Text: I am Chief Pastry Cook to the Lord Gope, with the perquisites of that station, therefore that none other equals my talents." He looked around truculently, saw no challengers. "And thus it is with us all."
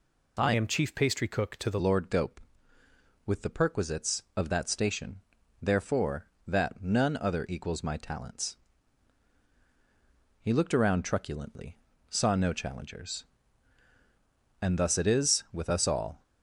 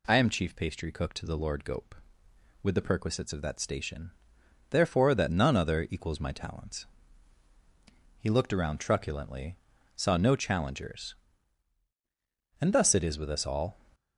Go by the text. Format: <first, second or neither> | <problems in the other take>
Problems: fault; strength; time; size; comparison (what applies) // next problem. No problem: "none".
second | changes voice from "am" to "the"; from 0.5 to 1.7 s; 1.2 s long